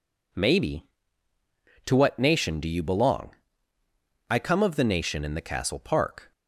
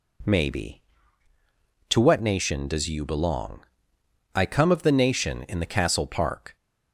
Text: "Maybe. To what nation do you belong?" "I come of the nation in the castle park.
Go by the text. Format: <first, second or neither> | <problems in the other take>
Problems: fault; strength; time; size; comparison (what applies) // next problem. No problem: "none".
first | says "does" for "do"; at 2.6 s